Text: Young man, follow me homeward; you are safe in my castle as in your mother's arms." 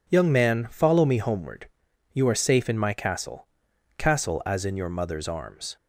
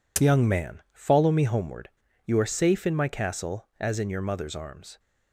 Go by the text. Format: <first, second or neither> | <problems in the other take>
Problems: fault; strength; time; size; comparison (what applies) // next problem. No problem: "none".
second | says "castle" twice; at 3.9 s